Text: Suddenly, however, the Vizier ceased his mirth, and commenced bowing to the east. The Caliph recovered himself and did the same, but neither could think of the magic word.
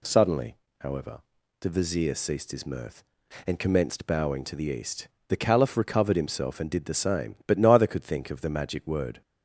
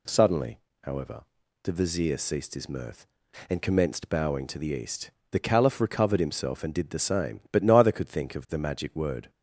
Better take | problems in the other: neither | none

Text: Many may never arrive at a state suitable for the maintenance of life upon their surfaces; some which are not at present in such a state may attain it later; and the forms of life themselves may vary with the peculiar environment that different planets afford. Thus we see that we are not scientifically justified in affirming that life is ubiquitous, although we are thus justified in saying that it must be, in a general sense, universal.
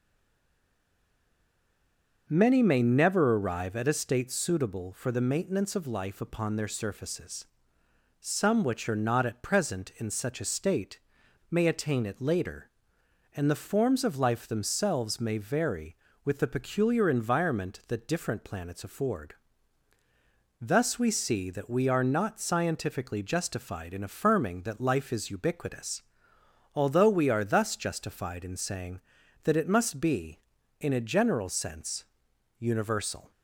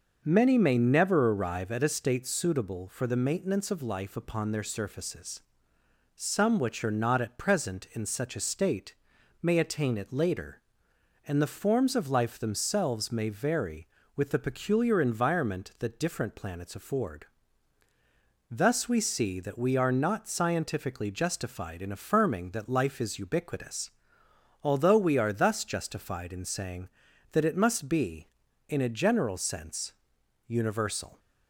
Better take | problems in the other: second | stays silent before the first word; until 2.2 s; 2.2 s long // starts louder than the rest; noticeable; until 3.2 s; 6 dB; noticeable in the second // pauses between "state" and "may"; noticeable; at 10.9 s; 0.49 s long; noticeable in the second

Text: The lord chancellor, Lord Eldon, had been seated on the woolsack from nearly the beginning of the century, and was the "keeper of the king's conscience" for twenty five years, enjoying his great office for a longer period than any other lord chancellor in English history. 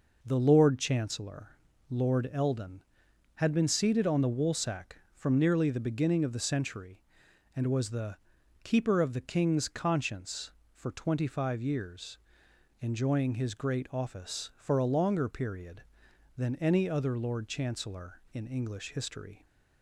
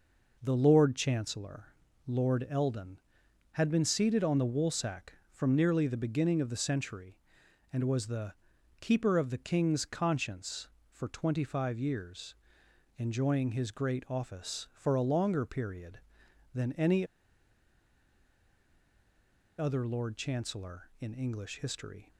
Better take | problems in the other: first | pauses between "the" and "keeper"; noticeable; at 8.3 s; 0.46 s long; noticeable in the first // pauses between "any" and "other"; strong; at 17.0 s; 2.5 s long

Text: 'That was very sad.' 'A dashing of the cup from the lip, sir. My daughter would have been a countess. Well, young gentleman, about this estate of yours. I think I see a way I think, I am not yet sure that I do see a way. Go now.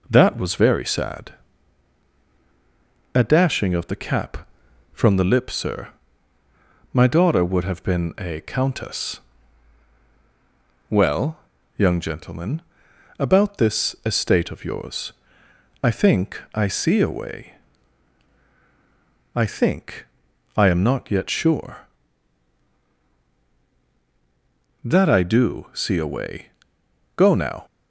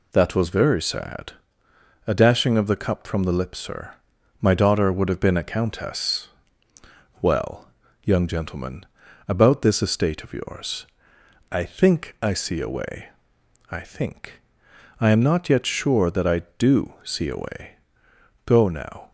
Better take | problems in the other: second | says "cap" for "cup"; at 3.9 s // pauses between "way" and "I"; strong; at 17.5 s; 1.8 s long; noticeable in the second

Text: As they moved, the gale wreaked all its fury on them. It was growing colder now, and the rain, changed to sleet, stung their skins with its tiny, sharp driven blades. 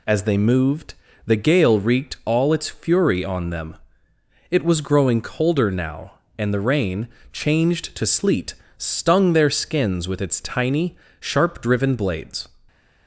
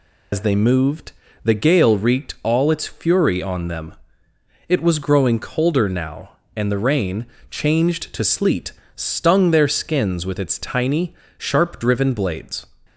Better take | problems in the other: first | loses the start of "As"; at 0.3 s; 85 ms

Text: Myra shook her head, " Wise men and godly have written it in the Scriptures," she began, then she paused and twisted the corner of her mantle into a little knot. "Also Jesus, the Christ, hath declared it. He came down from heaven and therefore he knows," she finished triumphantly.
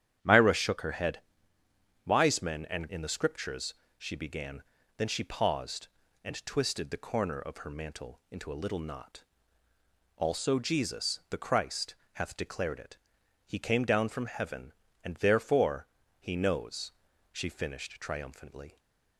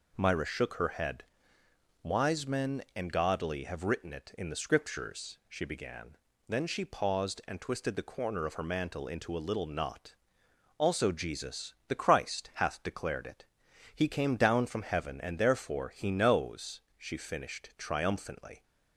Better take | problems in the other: second | starts louder than the rest; strong; until 1.2 s; 10 dB // skips "godly have written it"; at 2.8 s // pauses between "therefore" and "he"; slight; at 15.8 s; 0.32 s long

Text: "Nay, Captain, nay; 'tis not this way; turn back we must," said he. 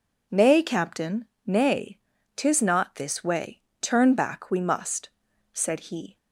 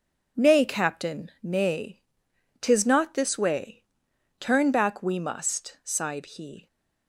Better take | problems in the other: first | says "sighed" for "said"; at 5.8 s

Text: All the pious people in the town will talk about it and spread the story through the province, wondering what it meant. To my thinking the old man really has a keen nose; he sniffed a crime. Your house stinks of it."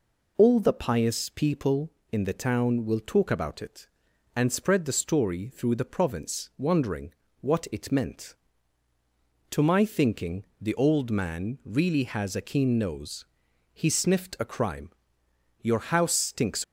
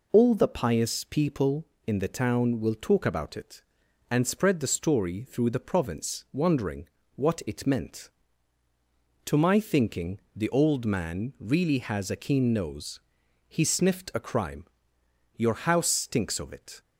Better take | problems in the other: second | pauses between "wondering" and "what"; slight; at 7.1 s; 0.28 s long; slight in the second // stops before "of it"; at 16.6 s

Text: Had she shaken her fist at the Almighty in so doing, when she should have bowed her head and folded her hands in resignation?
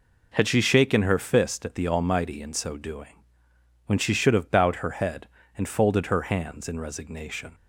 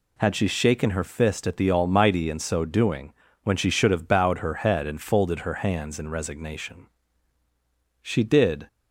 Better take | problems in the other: first | goes on to say "She did"; noticeable; from 8.0 s on; 0.66 s long

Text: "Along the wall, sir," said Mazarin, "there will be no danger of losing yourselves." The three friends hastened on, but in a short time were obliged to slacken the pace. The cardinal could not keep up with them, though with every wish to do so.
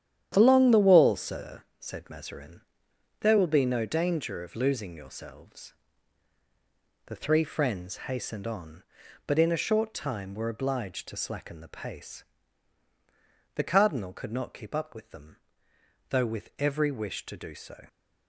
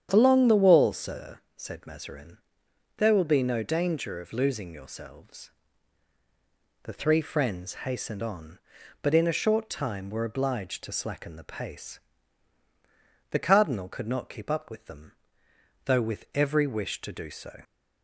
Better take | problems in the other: second | gets quieter; strong; throughout; 8 dB // starts louder than the rest; strong; until 1.3 s; 10 dB; strong in the second

